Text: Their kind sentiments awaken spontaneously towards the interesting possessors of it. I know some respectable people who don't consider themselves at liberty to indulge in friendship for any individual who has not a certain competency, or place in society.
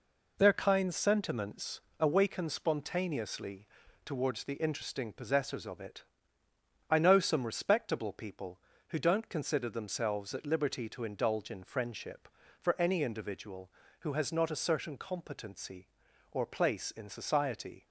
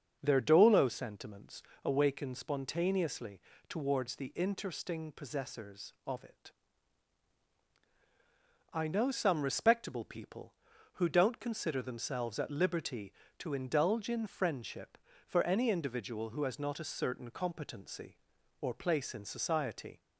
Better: first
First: pauses between "sentiments" and "awaken"; slight; at 1.7 s; 0.20 s long // pauses between "spontaneously" and "towards"; slight; at 3.6 s; 0.36 s long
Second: starts louder than the rest; until 1.2 s; 6.5 dB // says "dolo" for "kind"; at 0.4 s // pauses between "sentiments" and "awaken"; slight; at 1.6 s; 0.24 s long // pauses between "spontaneously" and "towards"; slight; at 3.3 s; 0.30 s long

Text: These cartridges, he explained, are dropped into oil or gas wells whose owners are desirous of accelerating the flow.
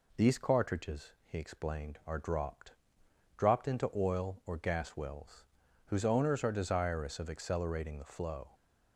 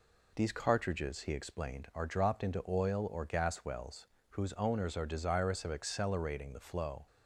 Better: second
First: says "dropped" twice; at 3.3 s // pauses between "wells" and "whose"; at 5.4 s; 0.40 s long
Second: pauses between "wells" and "whose"; slight; at 4.0 s; 0.28 s long

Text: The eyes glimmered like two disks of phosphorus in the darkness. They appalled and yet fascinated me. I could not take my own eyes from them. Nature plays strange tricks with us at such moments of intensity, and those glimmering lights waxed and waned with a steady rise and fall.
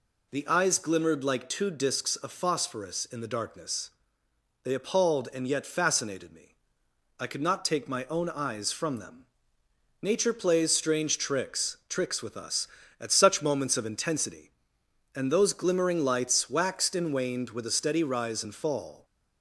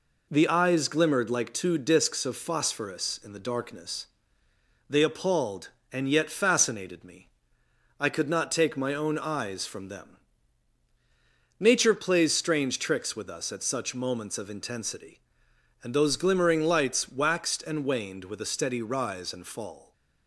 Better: second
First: says "tricks" twice; at 11.8 s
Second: none

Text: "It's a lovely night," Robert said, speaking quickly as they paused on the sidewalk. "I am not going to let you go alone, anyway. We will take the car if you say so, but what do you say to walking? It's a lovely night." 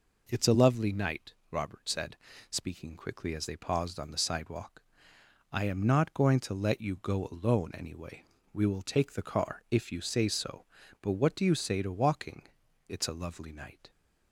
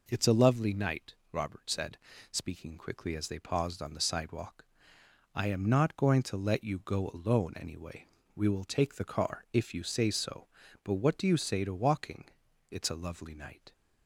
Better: neither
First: none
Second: none

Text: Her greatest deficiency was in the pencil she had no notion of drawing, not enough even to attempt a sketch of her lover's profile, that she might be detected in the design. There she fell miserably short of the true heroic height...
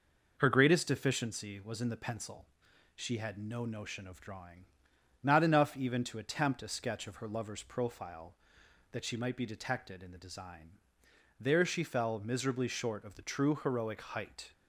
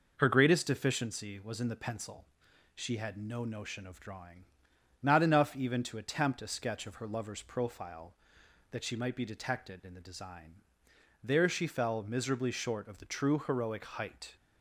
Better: neither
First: pauses between "pencil" and "she"; noticeable; at 2.4 s; 0.48 s long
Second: pauses between "pencil" and "she"; noticeable; at 2.2 s; 0.48 s long

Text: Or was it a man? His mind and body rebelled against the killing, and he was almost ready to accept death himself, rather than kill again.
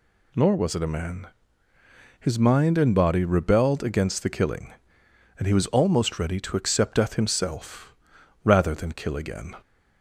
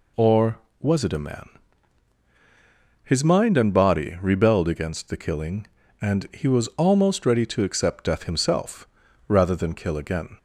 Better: second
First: says "Nor" for "Or"; at 0.3 s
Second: none

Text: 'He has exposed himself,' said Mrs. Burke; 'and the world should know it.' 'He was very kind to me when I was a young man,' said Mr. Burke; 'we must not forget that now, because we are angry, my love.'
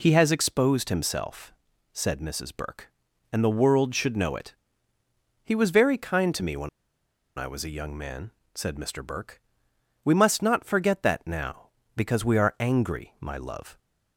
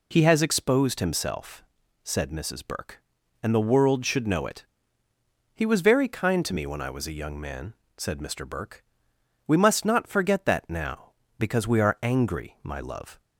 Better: second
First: pauses between "when" and "I"; noticeable; at 6.6 s; 0.69 s long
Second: none

